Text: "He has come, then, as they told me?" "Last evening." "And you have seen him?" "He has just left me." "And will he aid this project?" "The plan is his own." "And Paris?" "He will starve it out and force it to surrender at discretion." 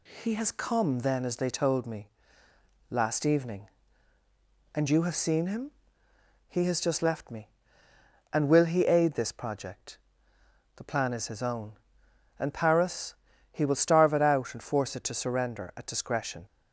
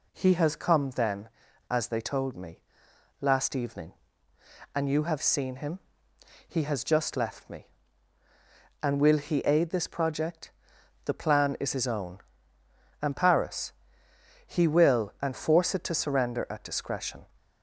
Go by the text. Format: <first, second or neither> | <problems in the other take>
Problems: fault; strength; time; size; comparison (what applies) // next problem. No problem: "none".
first | skips "starve it out"; at 15.1 s